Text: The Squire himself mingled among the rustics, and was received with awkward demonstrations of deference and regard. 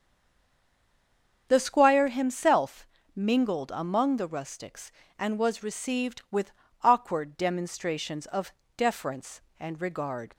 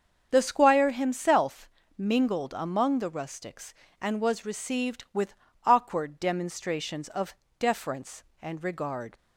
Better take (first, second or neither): second